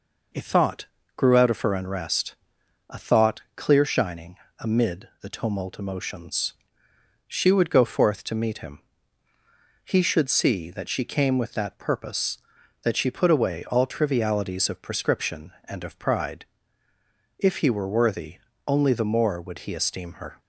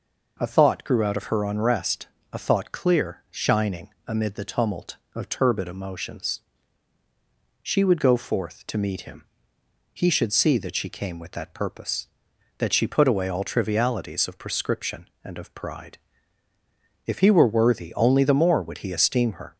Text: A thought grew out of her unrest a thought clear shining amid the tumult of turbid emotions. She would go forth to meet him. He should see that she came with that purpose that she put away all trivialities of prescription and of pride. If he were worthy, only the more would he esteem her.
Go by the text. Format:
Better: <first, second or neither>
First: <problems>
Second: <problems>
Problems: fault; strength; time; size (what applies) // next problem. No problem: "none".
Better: second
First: pauses between "thought" and "grew"; slight; at 0.8 s; 0.32 s long // pauses between "unrest" and "a"; noticeable; at 2.3 s; 0.52 s long // pauses between "shining" and "amid"; slight; at 4.3 s; 0.24 s long // skips "of turbid"; at 5.7 s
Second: pauses between "unrest" and "a"; slight; at 2.0 s; 0.26 s long // pauses between "shining" and "amid"; slight; at 3.8 s; 0.18 s long